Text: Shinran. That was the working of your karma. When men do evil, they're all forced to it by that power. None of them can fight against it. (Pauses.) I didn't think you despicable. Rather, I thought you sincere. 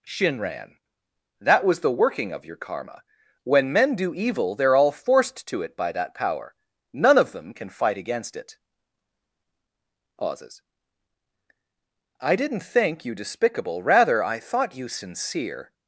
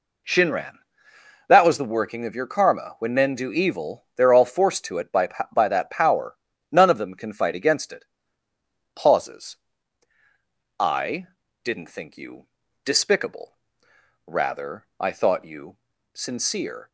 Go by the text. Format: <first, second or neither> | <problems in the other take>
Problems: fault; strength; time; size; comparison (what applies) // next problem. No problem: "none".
first | says "by" twice; at 5.5 s // pauses between "I" and "didn't"; slight; at 11.2 s; 0.36 s long // pauses between "you" and "despicable"; at 12.4 s; 0.40 s long // pauses between "you" and "sincere"; at 15.7 s; 0.38 s long